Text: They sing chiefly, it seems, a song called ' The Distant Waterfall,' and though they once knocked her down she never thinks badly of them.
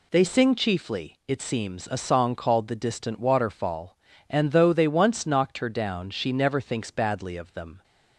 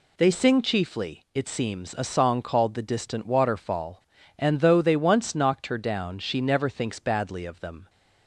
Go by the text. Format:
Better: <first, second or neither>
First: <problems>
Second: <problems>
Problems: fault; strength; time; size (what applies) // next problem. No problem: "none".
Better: neither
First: none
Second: none